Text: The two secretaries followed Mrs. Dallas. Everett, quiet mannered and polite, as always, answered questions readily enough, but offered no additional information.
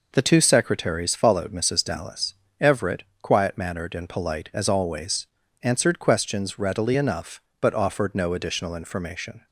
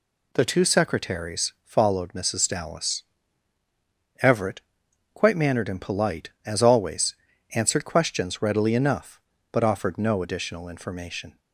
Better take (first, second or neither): first